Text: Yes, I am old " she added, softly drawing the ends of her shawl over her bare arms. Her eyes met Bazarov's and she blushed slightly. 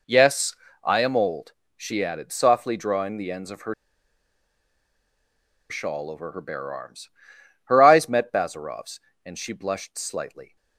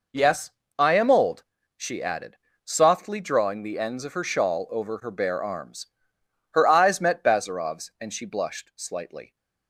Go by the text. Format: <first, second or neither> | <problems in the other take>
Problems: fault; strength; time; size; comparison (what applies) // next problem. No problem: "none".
second | pauses between "her" and "shawl"; strong; at 3.7 s; 1.9 s long